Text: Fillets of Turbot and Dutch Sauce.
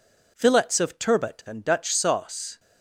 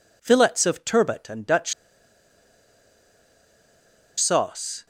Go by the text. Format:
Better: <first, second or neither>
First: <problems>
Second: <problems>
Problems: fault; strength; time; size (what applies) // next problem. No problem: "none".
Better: first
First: none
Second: pauses between "Dutch" and "Sauce"; strong; at 1.7 s; 2.4 s long